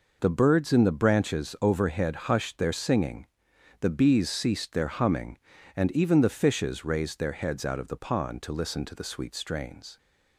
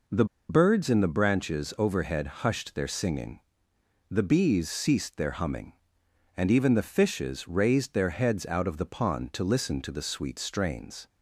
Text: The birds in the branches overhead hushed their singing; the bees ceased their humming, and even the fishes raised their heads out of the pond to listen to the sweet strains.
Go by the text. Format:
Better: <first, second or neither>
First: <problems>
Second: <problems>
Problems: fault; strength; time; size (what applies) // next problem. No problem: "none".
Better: first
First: none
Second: pauses between "The" and "birds"; slight; at 0.2 s; 0.24 s long // pauses between "overhead" and "hushed"; slight; at 2.2 s; 0.18 s long